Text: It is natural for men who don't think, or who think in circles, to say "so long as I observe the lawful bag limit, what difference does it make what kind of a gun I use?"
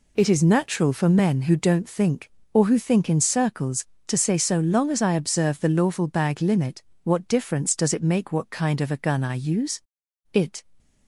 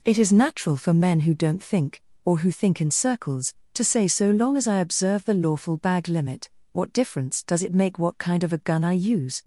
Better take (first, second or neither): second